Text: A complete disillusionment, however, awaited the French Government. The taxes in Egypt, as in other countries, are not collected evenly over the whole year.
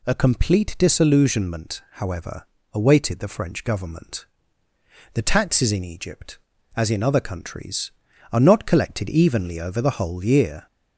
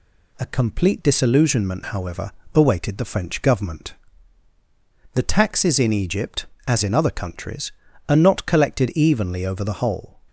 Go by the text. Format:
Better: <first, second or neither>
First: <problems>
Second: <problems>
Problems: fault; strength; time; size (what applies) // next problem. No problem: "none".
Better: first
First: none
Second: stops before "year"; at 10.2 s